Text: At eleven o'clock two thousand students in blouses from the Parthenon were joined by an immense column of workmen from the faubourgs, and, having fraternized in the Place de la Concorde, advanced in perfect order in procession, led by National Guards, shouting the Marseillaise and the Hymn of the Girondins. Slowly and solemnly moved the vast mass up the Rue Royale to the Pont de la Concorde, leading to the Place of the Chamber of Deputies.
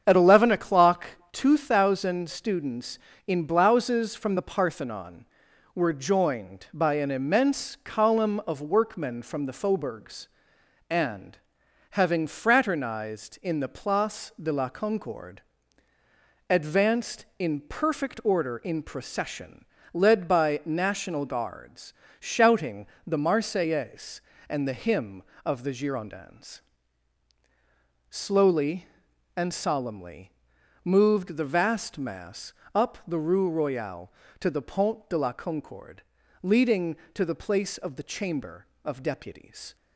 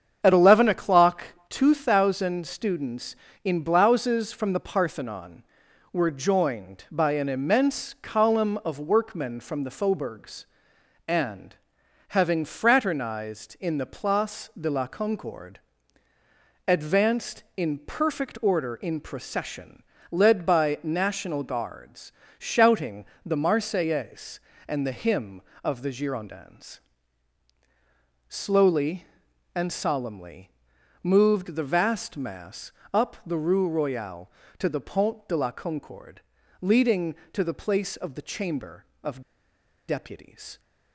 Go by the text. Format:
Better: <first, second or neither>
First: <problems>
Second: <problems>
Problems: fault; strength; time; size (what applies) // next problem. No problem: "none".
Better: first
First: starts louder than the rest; strong; until 1.0 s; 8 dB // pauses between "o'clock" and "two"; slight; at 1.0 s; 0.22 s long // pauses between "shouting" and "the"; slight; at 22.8 s; 0.20 s long // pauses between "solemnly" and "moved"; noticeable; at 30.3 s; 0.52 s long // pauses between "mass" and "up"; slight; at 32.5 s; 0.24 s long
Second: starts louder than the rest; strong; until 1.2 s; 8 dB // pauses between "o'clock" and "two"; slight; at 1.2 s; 0.22 s long // pauses between "shouting" and "the"; slight; at 23.0 s; 0.20 s long // pauses between "solemnly" and "moved"; noticeable; at 30.4 s; 0.52 s long // pauses between "mass" and "up"; slight; at 32.6 s; 0.24 s long // pauses between "of" and "Deputies"; noticeable; at 39.1 s; 0.68 s long